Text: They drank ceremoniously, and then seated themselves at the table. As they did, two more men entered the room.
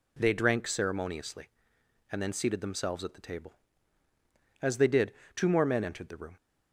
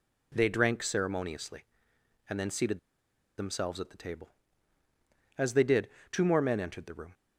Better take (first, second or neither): first